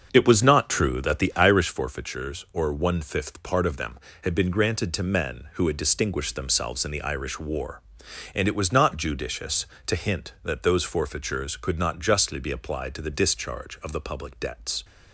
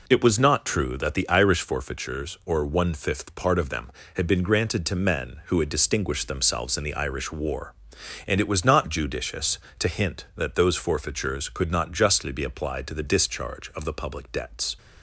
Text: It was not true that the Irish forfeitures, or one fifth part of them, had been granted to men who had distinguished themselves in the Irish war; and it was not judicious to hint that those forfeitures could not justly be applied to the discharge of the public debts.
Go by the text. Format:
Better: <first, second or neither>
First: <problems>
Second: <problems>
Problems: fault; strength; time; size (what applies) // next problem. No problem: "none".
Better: second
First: starts louder than the rest; until 1.6 s; 6.5 dB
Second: none